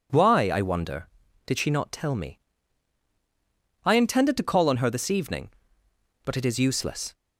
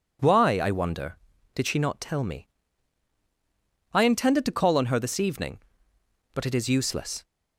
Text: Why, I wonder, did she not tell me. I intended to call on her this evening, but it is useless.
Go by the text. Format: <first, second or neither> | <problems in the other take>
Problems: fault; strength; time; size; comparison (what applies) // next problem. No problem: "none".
neither | none